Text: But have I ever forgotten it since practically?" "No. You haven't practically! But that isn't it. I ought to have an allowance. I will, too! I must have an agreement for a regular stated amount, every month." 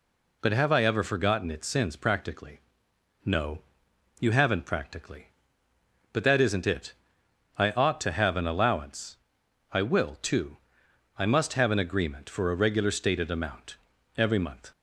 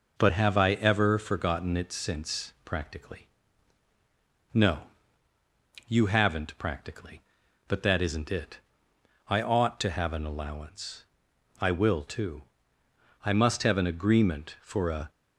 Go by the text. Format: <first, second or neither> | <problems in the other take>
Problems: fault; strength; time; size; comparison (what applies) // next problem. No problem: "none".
first | stops before "regular stated amount every month"; at 15.0 s